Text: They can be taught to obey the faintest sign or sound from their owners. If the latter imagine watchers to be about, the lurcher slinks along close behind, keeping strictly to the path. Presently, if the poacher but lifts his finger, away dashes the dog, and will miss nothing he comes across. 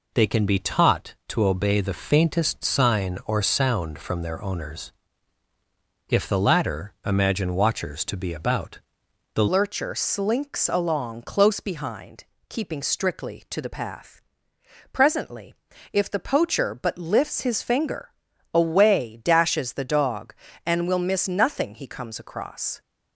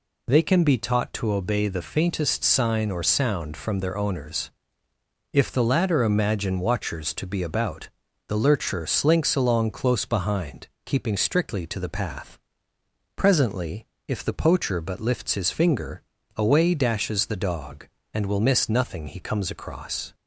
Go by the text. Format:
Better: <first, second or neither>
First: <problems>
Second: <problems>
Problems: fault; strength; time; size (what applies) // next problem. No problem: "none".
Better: second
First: changes voice at "lurcher"; from 9.4 s on; 13.4 s long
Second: none